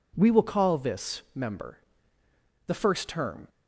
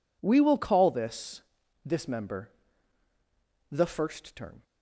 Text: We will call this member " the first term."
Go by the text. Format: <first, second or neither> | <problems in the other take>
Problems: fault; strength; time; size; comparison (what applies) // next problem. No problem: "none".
first | says "this" twice; at 1.8 s